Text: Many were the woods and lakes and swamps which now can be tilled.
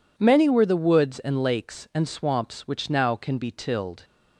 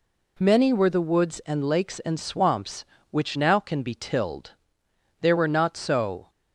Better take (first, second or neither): first